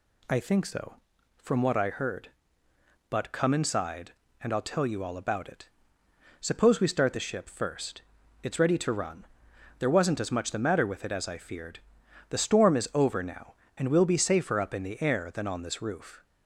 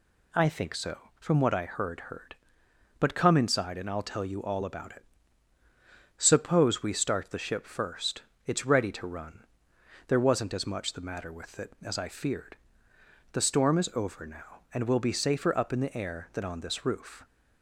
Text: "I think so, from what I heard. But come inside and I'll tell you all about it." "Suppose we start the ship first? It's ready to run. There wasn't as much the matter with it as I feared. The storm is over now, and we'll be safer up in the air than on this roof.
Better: first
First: none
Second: says "heard" twice; at 2.0 s

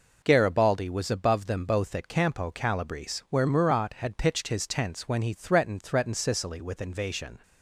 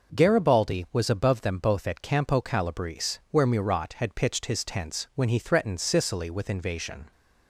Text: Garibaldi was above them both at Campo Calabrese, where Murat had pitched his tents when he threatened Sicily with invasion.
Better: second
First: says "threatened" twice; at 5.8 s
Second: none

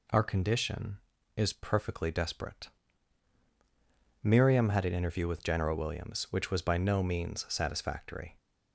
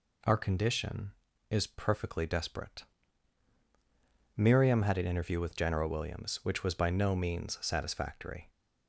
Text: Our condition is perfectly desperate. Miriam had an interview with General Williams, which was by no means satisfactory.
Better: neither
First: none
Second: none

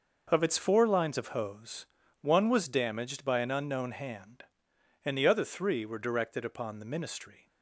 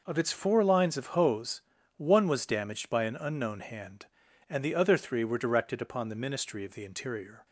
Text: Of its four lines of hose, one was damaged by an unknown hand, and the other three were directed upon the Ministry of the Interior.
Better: second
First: stops before "of the Interior"; at 7.4 s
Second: none

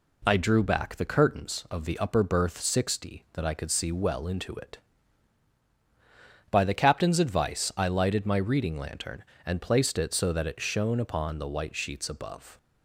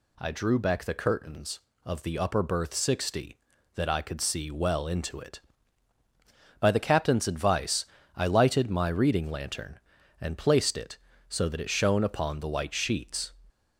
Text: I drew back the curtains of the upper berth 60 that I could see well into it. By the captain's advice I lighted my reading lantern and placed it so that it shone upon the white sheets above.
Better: first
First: none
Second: pauses between "advice" and "I"; slight; at 7.8 s; 0.32 s long // stops before "above"; at 13.5 s

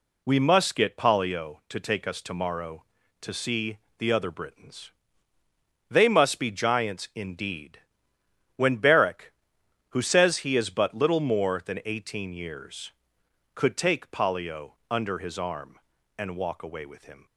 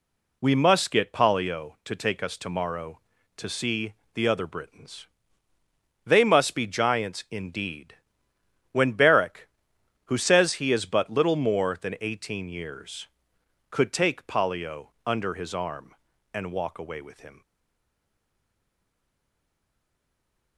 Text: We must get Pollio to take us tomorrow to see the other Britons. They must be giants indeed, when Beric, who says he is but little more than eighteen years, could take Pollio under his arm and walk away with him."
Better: first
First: pauses between "see" and "the"; slight; at 3.7 s; 0.18 s long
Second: pauses between "see" and "the"; slight; at 3.9 s; 0.18 s long // stays silent after the last word; strong; from 17.4 s on; 3.1 s long

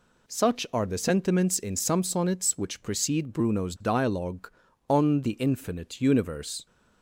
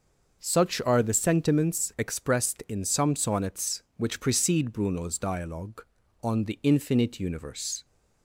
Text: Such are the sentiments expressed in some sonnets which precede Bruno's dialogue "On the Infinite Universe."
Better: second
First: skips "expressed"; at 1.5 s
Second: none

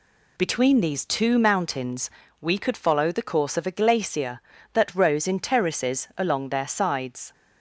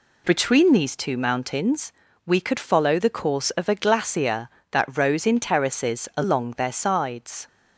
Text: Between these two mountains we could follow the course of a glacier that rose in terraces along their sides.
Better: neither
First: pauses between "mountains" and "we"; slight; at 2.1 s; 0.32 s long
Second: pauses between "mountains" and "we"; slight; at 1.9 s; 0.34 s long

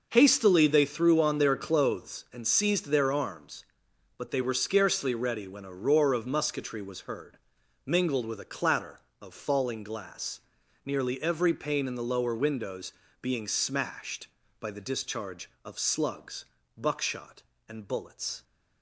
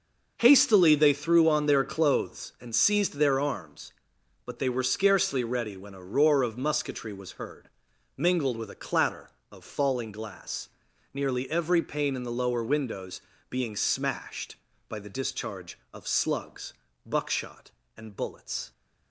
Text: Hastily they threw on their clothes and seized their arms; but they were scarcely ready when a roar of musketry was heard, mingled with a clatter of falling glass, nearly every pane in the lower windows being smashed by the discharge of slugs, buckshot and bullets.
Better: neither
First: starts louder than the rest; noticeable; until 1.1 s; 6 dB // pauses between "windows" and "being"; slight; at 12.9 s; 0.28 s long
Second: starts louder than the rest; noticeable; until 1.3 s; 6 dB // pauses between "windows" and "being"; slight; at 13.1 s; 0.28 s long

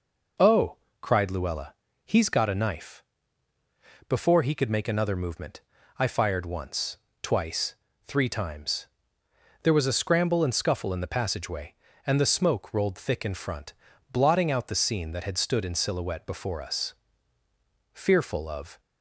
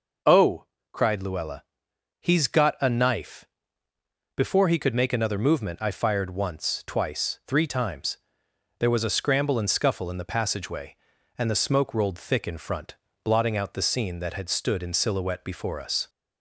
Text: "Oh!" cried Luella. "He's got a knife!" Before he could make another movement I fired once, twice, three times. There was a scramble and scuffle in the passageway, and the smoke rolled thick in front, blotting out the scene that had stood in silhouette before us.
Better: second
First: pauses between "movement" and "I"; at 5.6 s; 0.38 s long // goes on to say "Fearful of"; noticeable; from 17.9 s on; 0.86 s long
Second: none

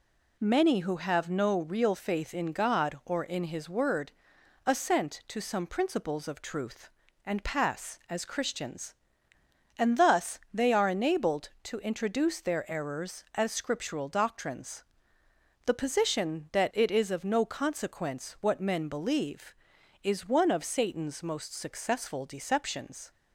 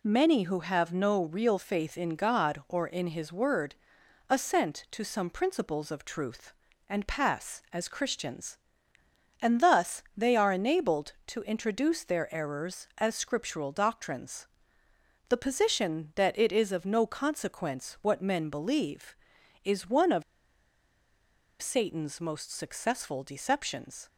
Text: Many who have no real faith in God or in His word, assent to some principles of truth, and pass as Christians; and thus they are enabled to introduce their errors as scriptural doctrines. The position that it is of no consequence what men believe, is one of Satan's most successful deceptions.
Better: first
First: none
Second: pauses between "of" and "Satan's"; strong; at 20.2 s; 1.3 s long

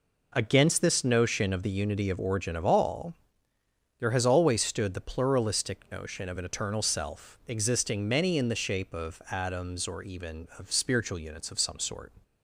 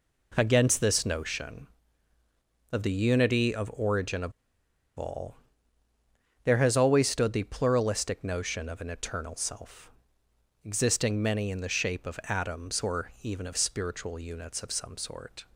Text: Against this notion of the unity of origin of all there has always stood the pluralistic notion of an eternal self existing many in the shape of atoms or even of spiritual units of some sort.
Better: first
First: pauses between "all" and "there"; noticeable; at 3.1 s; 0.86 s long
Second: pauses between "of" and "all"; noticeable; at 4.3 s; 0.64 s long // pauses between "all" and "there"; at 5.3 s; 1.0 s long // pauses between "self" and "existing"; noticeable; at 9.9 s; 0.74 s long

